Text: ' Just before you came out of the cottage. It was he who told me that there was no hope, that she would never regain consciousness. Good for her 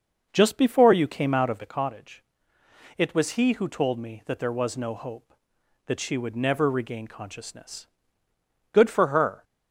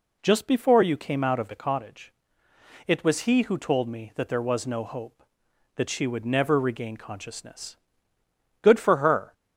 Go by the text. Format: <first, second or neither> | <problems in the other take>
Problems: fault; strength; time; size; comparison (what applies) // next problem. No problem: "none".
second | starts louder than the rest; noticeable; until 1.7 s; 6 dB